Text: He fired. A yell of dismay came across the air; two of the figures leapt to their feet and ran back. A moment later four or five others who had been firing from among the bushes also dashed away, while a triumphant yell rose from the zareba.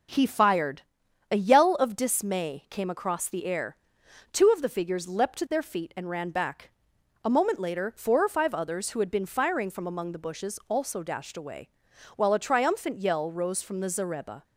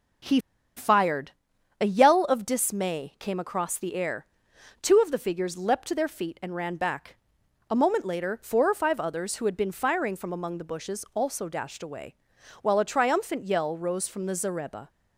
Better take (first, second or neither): first